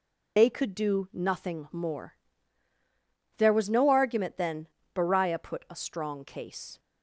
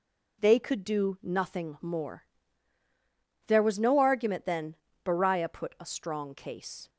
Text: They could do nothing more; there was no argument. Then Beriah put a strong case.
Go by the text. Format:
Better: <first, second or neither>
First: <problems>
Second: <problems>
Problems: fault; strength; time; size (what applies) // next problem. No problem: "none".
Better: second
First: loses the start of "They"; at 0.3 s; 55 ms // pauses between "Then" and "Beriah"; slight; at 4.6 s; 0.26 s long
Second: pauses between "Then" and "Beriah"; slight; at 4.7 s; 0.28 s long